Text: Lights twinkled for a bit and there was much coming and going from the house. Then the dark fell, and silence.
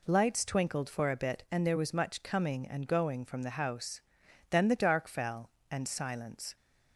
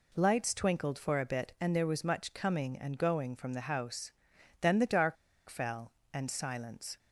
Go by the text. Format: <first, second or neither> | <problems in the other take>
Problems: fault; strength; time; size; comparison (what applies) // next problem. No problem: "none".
first | pauses between "dark" and "fell"; slight; at 5.1 s; 0.32 s long